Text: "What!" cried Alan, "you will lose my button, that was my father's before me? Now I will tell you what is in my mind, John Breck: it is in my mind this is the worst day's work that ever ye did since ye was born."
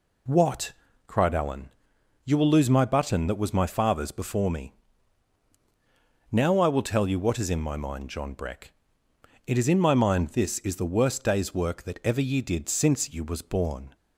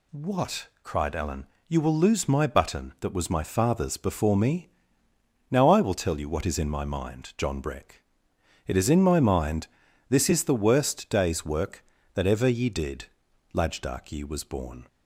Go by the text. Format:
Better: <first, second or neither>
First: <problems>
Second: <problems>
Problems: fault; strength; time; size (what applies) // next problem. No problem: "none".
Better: first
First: none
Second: pauses between "mind" and "this"; at 9.6 s; 0.42 s long // says "lajdak" for "since"; at 13.5 s